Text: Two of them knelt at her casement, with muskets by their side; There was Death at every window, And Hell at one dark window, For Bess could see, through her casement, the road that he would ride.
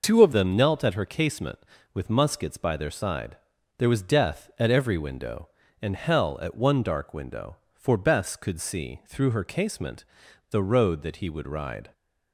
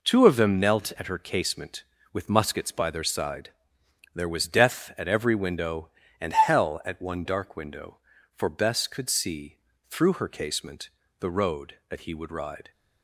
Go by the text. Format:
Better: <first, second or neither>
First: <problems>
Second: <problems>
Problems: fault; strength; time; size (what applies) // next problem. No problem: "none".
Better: second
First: changes voice at "them"; from 0.3 s on; 11.6 s long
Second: none